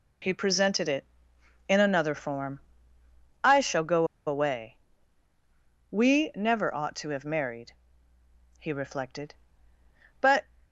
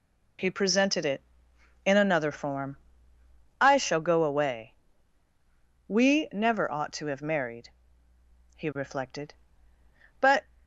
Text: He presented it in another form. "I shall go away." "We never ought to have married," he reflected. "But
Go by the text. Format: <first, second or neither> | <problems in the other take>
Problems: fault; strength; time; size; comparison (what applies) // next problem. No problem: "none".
second | pauses between "go" and "away"; slight; at 4.0 s; 0.20 s long